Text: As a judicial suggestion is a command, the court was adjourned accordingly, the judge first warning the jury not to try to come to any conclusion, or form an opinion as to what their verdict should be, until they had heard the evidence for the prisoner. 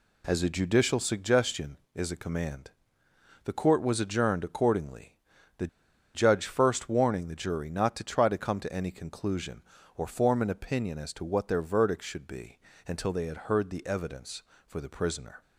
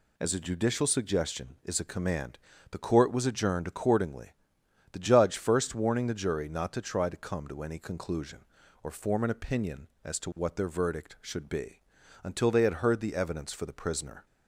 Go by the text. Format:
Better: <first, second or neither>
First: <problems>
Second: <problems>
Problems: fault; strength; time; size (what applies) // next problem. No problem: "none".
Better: second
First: pauses between "the" and "judge"; noticeable; at 5.6 s; 0.47 s long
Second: none